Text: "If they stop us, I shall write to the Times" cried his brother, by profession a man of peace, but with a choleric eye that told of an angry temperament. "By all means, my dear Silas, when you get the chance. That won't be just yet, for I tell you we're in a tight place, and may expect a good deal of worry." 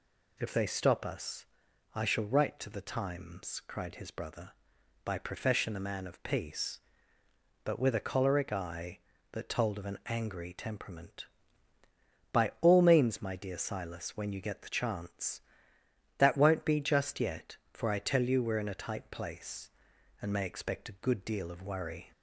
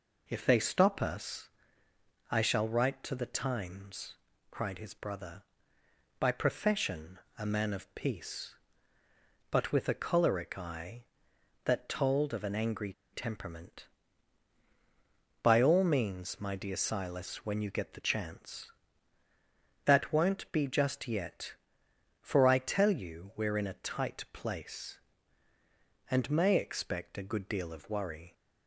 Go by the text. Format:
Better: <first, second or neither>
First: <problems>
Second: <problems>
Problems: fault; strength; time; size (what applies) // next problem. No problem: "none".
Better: first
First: none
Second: pauses between "Times" and "cried"; slight; at 4.1 s; 0.34 s long // pauses between "profession" and "a"; slight; at 7.2 s; 0.18 s long // pauses between "angry" and "temperament"; slight; at 12.9 s; 0.20 s long